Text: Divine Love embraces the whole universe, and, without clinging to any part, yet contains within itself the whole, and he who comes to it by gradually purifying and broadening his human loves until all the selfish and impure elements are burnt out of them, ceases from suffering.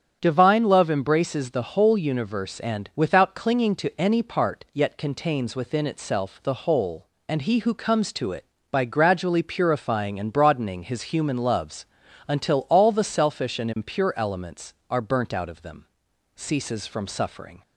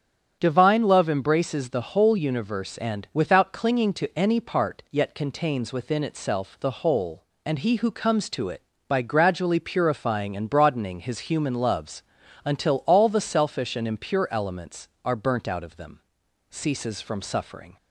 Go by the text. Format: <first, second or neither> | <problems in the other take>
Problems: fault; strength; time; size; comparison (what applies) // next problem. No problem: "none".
neither | starts louder than the rest; strong; the same in both // pauses between "loves" and "until"; the same in both